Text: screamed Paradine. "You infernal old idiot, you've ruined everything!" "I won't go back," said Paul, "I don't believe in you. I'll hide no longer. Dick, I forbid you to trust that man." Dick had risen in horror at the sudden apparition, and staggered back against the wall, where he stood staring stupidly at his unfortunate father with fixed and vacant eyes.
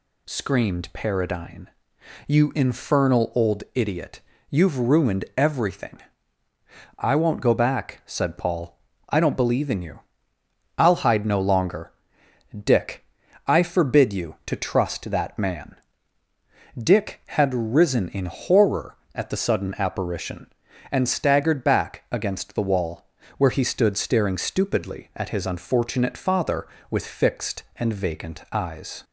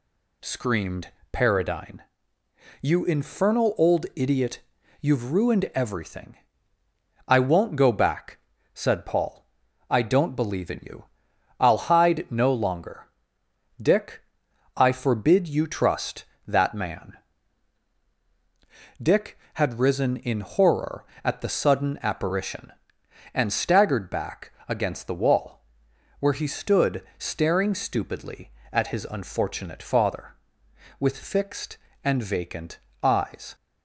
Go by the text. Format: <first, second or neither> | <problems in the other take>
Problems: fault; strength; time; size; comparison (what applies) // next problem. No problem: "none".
first | pauses between "screamed" and "Paradine"; slight; at 1.1 s; 0.20 s long // skips "to"; at 15.6 s // pauses between "back" and "against"; slight; at 24.5 s; 0.16 s long // pauses between "vacant" and "eyes"; slight; at 32.7 s; 0.24 s long